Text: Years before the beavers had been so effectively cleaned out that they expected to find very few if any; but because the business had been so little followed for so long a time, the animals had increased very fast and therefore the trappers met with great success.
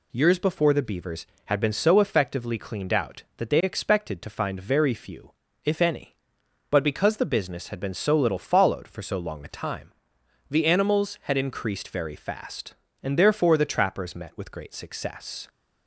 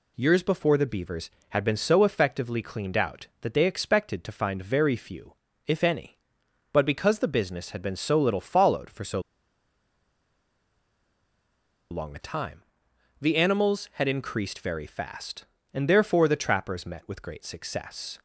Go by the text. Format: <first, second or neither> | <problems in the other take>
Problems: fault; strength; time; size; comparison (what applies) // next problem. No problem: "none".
first | pauses between "few" and "if"; slight; at 5.3 s; 0.32 s long; slight in the first // pauses between "so" and "long"; strong; at 9.1 s; 2.7 s long